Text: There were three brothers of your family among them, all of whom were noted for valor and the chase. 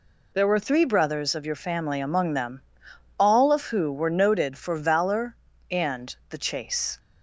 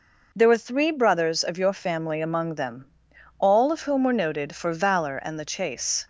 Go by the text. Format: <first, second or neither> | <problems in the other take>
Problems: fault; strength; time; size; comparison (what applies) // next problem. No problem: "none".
second | says "who" for "whom"; at 3.6 s